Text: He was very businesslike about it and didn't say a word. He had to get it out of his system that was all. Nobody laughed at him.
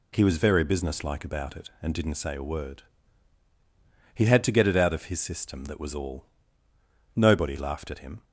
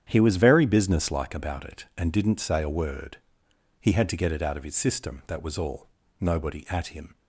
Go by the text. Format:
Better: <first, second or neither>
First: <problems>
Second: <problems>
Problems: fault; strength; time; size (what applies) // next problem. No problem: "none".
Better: first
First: none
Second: starts louder than the rest; strong; until 1.1 s; 9 dB // skips "laughed"; at 6.6 s